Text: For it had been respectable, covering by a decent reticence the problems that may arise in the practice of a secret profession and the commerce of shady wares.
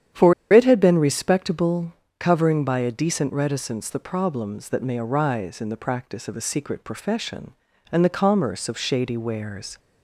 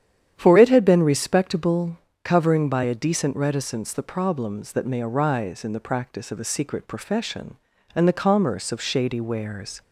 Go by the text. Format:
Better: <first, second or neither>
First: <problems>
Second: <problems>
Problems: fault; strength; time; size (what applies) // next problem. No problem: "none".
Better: second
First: starts louder than the rest; strong; until 1.3 s; 9.5 dB // pauses between "For" and "it"; slight; at 0.3 s; 0.19 s long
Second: starts louder than the rest; strong; until 1.3 s; 9.5 dB